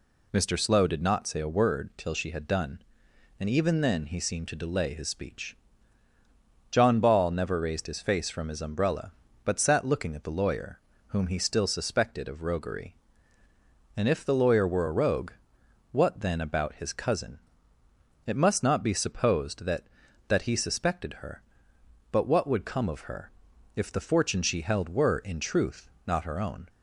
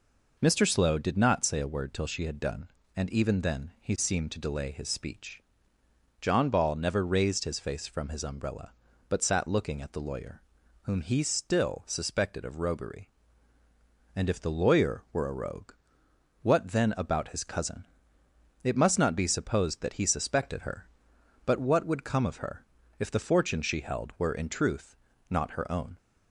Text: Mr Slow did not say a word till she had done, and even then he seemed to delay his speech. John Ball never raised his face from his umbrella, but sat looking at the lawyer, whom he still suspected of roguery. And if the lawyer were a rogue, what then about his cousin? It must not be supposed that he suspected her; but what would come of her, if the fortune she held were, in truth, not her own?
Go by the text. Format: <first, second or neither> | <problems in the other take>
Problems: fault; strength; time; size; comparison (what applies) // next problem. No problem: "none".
second | says "that" twice; at 20.2 s